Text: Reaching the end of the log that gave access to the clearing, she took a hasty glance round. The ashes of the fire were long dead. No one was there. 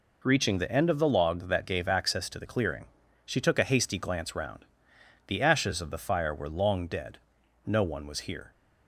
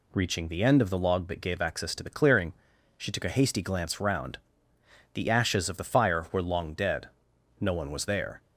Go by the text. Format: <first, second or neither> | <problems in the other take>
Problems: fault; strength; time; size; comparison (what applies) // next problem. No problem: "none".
second | says "here" for "there"; at 8.2 s